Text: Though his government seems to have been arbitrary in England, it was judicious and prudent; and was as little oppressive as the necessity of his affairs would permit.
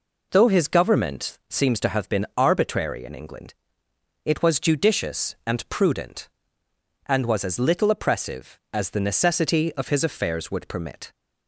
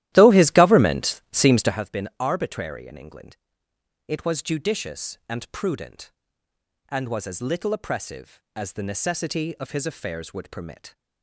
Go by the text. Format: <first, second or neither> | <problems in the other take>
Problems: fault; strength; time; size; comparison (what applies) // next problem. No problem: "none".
first | starts louder than the rest; strong; until 1.8 s; 14 dB